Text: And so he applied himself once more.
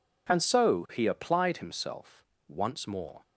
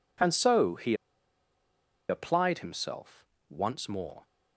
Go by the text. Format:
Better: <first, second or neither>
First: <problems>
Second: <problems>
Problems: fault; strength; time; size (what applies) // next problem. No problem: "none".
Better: first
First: pauses between "himself" and "once"; slight; at 2.2 s; 0.24 s long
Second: pauses between "he" and "applied"; at 0.9 s; 1.1 s long // pauses between "himself" and "once"; slight; at 3.2 s; 0.24 s long